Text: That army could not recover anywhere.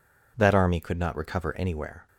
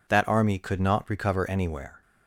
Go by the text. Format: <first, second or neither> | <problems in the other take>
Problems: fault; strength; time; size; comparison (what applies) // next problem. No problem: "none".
neither | none